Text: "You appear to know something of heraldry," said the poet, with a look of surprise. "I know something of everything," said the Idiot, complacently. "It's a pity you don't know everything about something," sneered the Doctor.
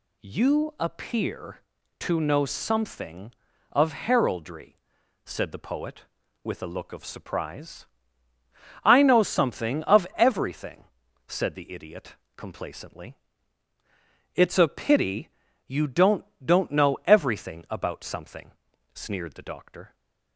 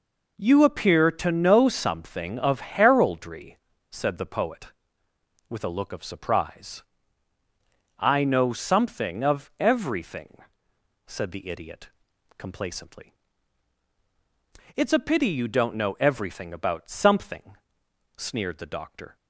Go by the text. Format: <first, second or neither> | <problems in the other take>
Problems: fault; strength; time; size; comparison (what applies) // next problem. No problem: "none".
second | pauses between "pity" and "you"; at 15.2 s; 0.38 s long // says "don't" twice; at 16.4 s